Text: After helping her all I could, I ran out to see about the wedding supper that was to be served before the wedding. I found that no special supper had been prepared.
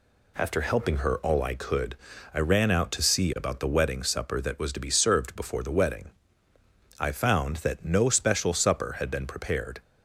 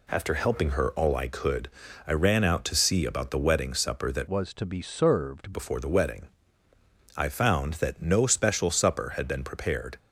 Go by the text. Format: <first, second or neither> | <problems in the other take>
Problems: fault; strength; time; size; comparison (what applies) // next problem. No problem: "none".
first | changes voice from "was" to "served"; from 4.2 to 5.5 s; 1.3 s long